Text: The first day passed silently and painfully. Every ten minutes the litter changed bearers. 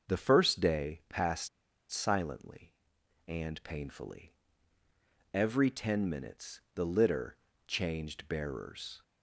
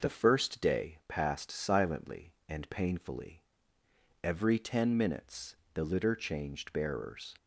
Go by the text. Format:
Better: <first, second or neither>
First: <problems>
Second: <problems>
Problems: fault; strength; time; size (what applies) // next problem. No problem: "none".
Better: second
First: starts louder than the rest; until 1.1 s; 6 dB // pauses between "passed" and "silently"; at 1.4 s; 0.43 s long // pauses between "minutes" and "the"; slight; at 6.6 s; 0.16 s long // pauses between "litter" and "changed"; slight; at 7.3 s; 0.30 s long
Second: pauses between "minutes" and "the"; slight; at 5.5 s; 0.20 s long